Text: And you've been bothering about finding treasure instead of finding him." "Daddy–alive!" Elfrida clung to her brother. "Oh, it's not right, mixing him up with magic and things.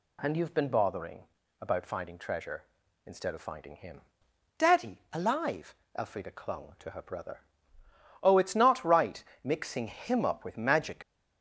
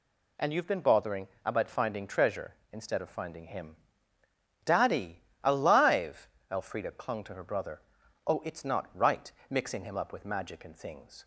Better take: second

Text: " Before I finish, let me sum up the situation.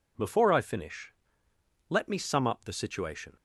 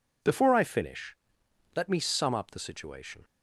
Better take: neither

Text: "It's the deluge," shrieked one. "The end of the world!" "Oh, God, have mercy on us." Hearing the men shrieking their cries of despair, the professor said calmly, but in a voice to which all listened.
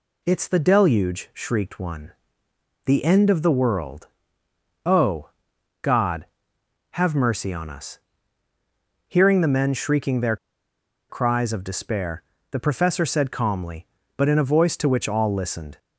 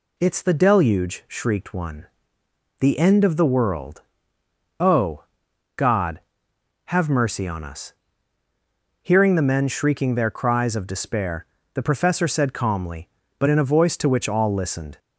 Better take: second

